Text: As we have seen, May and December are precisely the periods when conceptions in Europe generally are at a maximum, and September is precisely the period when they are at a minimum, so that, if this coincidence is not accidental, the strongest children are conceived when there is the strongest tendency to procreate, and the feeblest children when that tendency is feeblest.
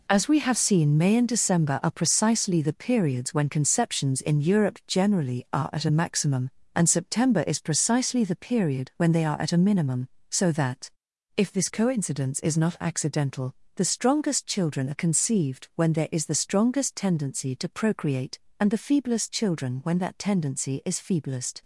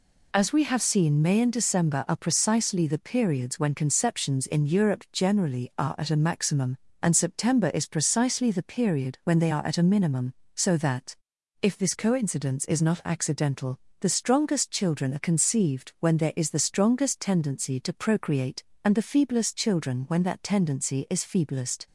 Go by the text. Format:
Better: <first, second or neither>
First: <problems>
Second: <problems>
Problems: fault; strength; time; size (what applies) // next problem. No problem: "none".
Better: second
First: gets quieter; strong; throughout; 8.5 dB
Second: none